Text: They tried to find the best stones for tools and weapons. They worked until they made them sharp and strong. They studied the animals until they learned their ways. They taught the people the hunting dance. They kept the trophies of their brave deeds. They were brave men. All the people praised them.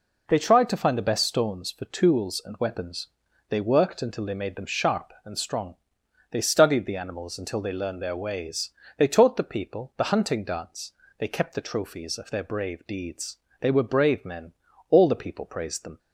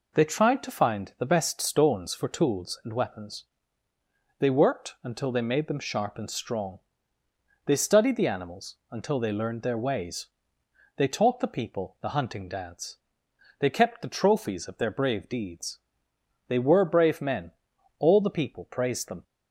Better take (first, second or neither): neither